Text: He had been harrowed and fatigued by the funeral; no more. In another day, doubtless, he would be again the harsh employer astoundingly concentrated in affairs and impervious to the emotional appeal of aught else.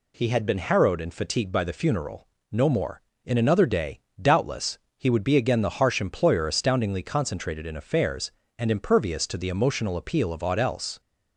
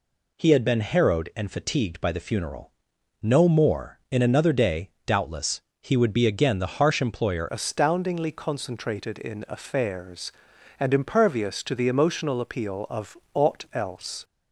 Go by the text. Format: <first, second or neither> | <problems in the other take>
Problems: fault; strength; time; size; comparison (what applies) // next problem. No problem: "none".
first | changes voice at "astoundingly"; from 7.4 s on; 6.8 s long // pauses between "of" and "aught"; slight; at 13.1 s; 0.16 s long